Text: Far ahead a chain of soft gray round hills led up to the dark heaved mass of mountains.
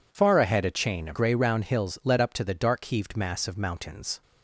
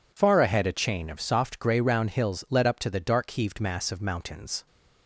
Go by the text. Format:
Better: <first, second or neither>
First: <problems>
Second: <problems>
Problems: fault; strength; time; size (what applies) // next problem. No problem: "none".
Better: second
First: skips "soft"; at 1.1 s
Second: none